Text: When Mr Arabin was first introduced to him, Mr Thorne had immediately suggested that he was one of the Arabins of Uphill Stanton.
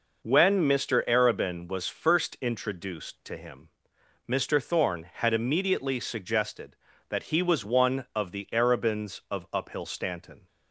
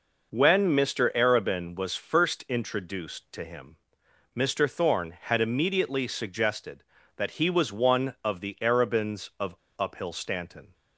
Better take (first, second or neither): first